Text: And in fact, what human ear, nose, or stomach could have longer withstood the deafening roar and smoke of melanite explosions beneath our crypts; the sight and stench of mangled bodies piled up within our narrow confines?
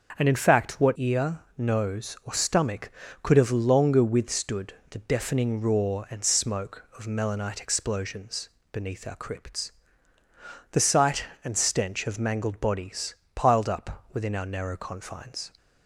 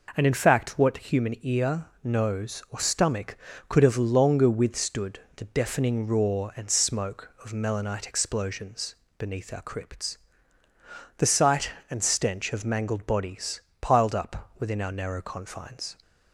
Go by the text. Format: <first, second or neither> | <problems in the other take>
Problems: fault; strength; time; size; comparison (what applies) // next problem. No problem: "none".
second | starts louder than the rest; until 1.2 s; 6.5 dB // skips "human"; at 0.9 s // pauses between "withstood" and "the"; slight; at 4.7 s; 0.16 s long; slight in the second // pauses between "explosions" and "beneath"; slight; at 8.4 s; 0.22 s long; slight in the second // pauses between "bodies" and "piled"; slight; at 13.1 s; 0.20 s long; slight in the second